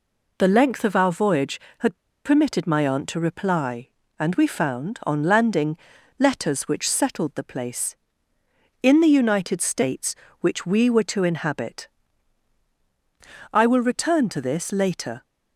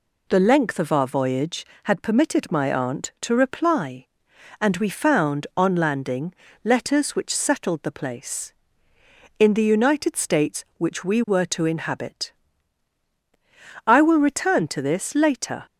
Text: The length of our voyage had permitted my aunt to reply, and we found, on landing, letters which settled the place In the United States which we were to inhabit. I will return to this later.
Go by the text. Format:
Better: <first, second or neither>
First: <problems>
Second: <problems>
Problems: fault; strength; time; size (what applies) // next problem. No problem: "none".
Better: second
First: pauses between "had" and "permitted"; slight; at 1.9 s; 0.27 s long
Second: none